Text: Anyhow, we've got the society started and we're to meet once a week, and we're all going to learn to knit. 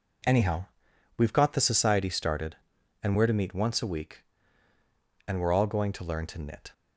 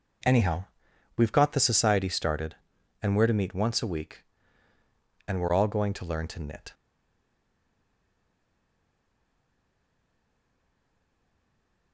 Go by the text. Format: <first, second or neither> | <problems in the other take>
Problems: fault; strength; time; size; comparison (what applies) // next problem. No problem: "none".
first | stays silent after the last word; strong; from 6.7 s on; 5.2 s long